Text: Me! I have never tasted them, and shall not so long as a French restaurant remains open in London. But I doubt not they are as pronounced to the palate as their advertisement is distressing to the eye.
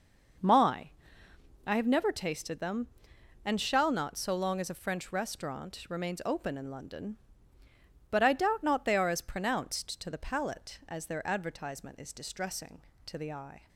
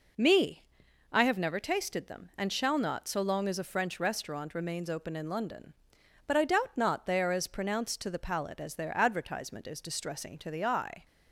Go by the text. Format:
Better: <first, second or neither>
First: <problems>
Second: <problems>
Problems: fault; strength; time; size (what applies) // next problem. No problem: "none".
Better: second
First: says "My" for "Me"; at 0.3 s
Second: none